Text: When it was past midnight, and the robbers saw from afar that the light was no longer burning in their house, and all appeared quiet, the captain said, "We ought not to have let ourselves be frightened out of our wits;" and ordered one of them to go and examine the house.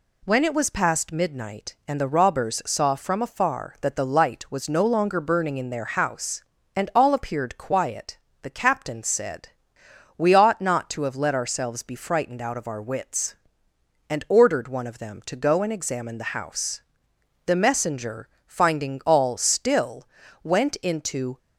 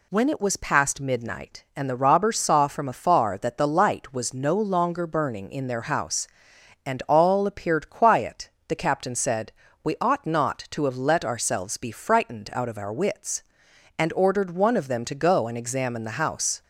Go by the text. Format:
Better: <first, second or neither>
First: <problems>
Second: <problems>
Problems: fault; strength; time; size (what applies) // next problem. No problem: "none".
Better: second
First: goes on to say "The messenger finding all still went into"; strong; from 17.4 s on; 3.9 s long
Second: none